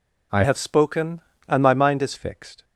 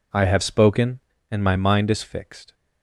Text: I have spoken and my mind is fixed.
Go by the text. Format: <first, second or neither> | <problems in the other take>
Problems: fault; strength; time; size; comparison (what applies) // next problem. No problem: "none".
second | changes voice from "have" to "is"; from 0.4 to 2.1 s; 1.7 s long